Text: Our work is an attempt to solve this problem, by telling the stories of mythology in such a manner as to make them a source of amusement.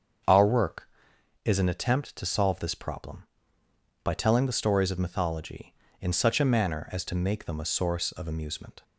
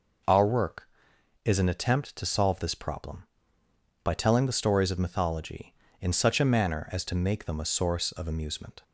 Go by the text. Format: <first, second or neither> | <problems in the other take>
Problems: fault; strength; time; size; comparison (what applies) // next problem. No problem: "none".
second | starts louder than the rest; until 1.2 s; 7 dB